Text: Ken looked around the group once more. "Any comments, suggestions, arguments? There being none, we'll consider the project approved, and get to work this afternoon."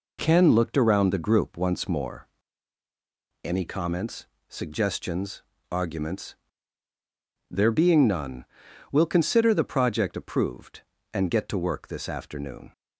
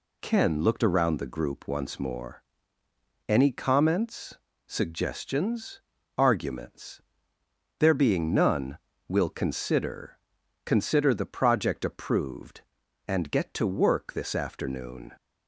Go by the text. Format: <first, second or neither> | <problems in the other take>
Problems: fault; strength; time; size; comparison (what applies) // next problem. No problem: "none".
first | says "consider" twice; at 10.6 s